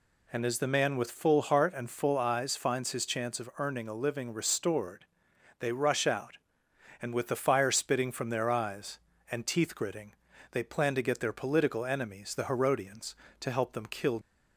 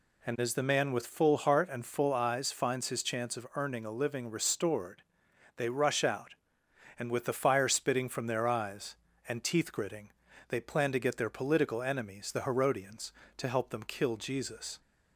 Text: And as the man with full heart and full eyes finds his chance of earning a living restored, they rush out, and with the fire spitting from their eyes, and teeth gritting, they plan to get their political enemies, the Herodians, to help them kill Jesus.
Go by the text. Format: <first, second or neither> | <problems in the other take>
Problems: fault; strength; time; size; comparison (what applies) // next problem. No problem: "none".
second | stops before "Jesus"; at 14.2 s